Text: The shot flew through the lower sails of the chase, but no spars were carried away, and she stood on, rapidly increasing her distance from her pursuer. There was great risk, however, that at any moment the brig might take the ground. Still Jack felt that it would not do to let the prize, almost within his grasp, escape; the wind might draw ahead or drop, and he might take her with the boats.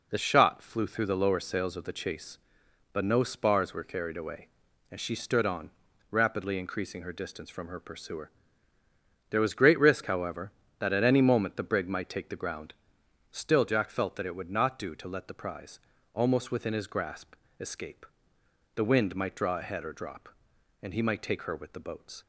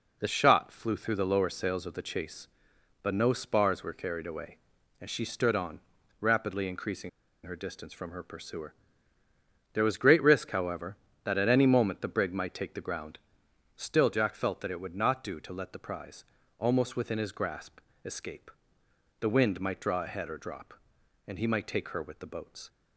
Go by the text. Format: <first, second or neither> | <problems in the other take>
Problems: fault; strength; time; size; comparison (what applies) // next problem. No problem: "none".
first | pauses between "increasing" and "her"; at 7.0 s; 0.36 s long